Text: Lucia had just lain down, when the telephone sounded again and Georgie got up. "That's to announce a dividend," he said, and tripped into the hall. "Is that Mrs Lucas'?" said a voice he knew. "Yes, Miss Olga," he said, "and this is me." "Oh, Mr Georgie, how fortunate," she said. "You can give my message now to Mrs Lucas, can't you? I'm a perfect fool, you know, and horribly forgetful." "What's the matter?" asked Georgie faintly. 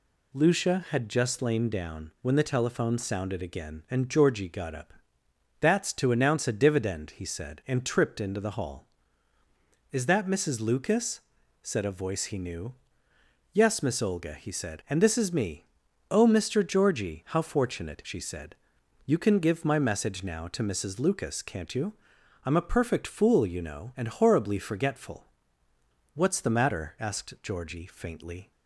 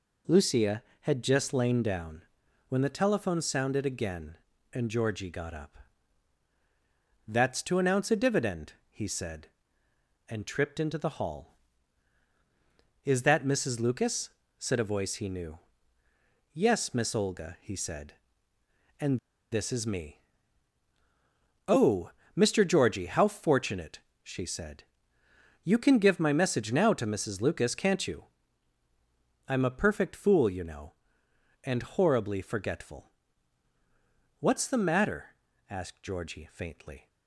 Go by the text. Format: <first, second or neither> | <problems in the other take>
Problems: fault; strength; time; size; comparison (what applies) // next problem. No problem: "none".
first | pauses between "and" and "this"; slight; at 19.1 s; 0.32 s long